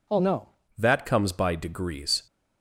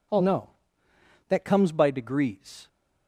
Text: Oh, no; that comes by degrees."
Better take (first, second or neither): second